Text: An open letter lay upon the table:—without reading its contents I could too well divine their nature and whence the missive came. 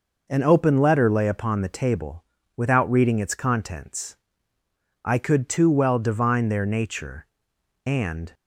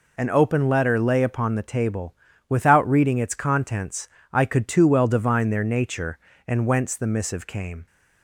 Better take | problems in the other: second | pauses between "contents" and "I"; noticeable; at 4.1 s; 0.84 s long; slight in the second // stops before "whence the missive came"; at 8.3 s

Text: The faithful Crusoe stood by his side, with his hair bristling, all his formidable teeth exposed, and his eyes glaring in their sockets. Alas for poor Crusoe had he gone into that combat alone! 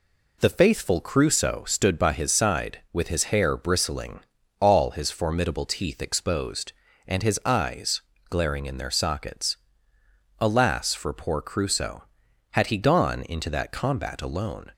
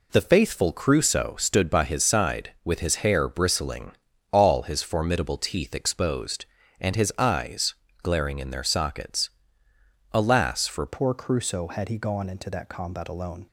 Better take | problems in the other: first | pauses between "eyes" and "glaring"; slight; at 7.7 s; 0.30 s long; slight in the first // changes voice at "poor"; from 10.8 s on; 2.6 s long

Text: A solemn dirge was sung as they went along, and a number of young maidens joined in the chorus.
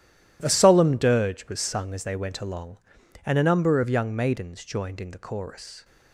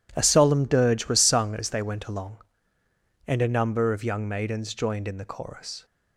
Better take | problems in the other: neither | none

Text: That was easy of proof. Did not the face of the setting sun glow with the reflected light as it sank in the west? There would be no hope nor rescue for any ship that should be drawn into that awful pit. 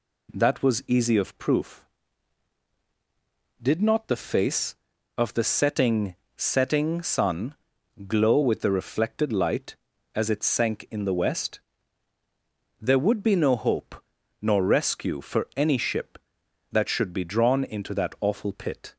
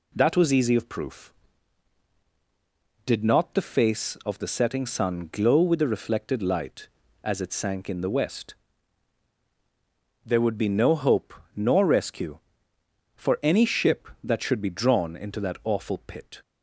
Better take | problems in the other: second | says "setting" twice; at 6.3 s // pauses between "sun" and "glow"; noticeable; at 7.5 s; 0.52 s long // pauses between "hope" and "nor"; noticeable; at 13.9 s; 0.46 s long; slight in the second

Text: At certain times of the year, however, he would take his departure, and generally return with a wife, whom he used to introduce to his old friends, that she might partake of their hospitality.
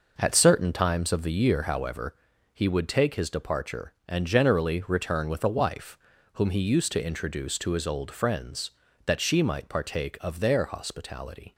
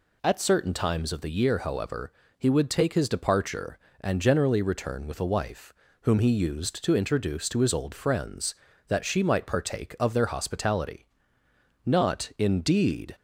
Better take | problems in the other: first | goes on to say "Not indeed"; noticeable; from 11.8 s on; 1.2 s long

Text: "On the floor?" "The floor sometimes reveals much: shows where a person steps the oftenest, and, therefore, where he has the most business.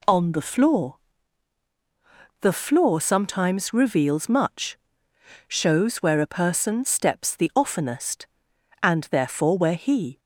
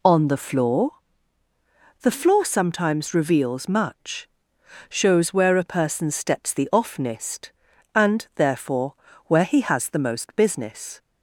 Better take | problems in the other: second | stops before "has the most business"; at 10.1 s

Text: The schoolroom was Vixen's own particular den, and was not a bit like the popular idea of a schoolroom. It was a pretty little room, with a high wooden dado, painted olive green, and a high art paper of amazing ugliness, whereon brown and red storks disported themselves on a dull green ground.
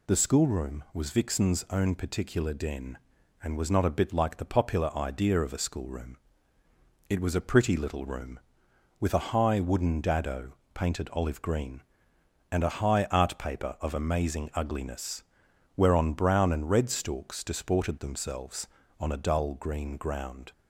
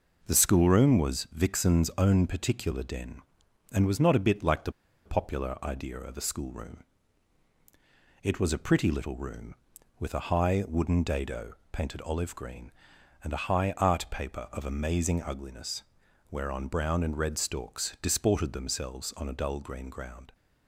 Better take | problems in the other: first | pauses between "the" and "popular"; slight; at 4.7 s; 0.34 s long

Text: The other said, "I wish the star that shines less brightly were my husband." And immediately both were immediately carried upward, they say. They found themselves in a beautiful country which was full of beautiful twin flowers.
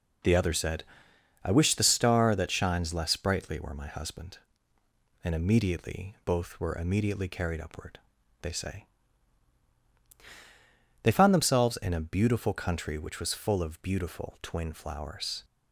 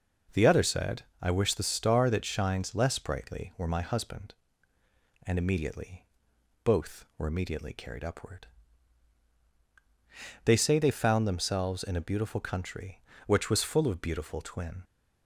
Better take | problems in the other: first | pauses between "immediately" and "both"; noticeable; at 6.0 s; 0.58 s long // stops before "flowers"; at 14.8 s

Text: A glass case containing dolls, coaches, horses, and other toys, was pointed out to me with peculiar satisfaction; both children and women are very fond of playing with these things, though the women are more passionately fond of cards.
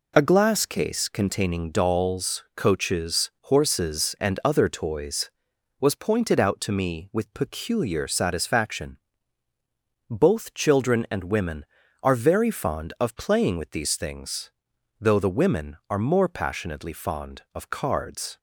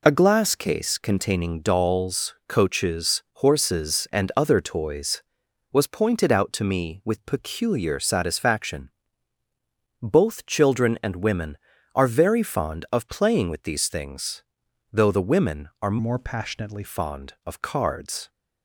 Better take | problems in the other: first | changes voice from "more" to "passionately"; from 15.9 to 16.8 s; 0.9 s long

